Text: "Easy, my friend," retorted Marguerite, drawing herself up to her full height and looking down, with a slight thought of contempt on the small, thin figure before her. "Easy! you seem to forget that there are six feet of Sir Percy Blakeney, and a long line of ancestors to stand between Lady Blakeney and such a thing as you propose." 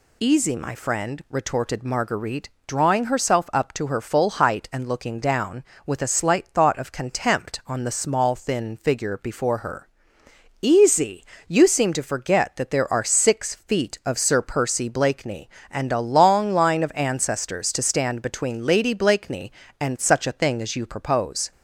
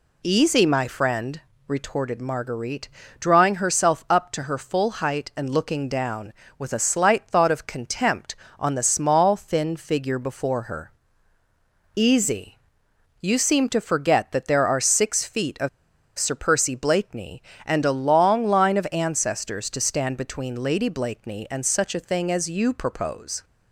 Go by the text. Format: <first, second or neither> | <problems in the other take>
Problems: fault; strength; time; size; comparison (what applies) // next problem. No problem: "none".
first | pauses between "of" and "Sir"; noticeable; at 15.6 s; 0.48 s long